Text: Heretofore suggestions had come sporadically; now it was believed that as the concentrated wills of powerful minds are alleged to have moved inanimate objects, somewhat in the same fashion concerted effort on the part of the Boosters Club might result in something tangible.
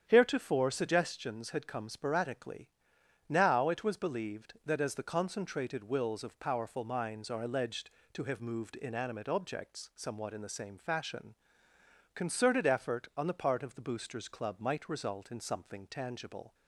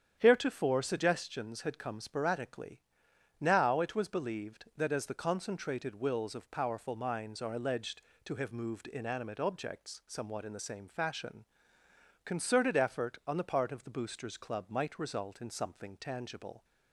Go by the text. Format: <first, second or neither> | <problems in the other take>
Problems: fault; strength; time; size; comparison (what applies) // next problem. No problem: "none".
neither | starts louder than the rest; strong; the same in both // pauses between "fashion" and "concerted"; noticeable; the same in both